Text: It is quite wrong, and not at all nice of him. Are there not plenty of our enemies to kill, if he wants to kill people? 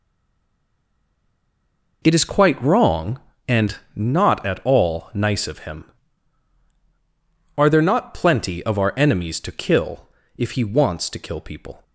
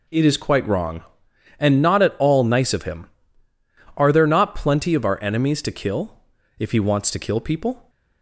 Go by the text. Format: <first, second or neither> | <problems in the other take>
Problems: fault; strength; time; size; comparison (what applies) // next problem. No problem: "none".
second | stays silent before the first word; noticeable; until 2.0 s; 2.0 s long // pauses between "and" and "not"; slight; at 3.7 s; 0.18 s long